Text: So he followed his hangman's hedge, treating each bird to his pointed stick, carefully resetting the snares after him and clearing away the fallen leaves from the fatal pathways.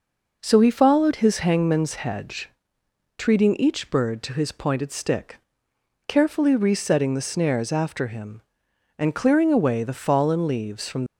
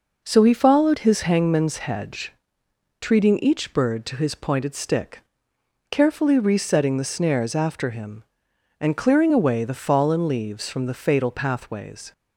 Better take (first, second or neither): second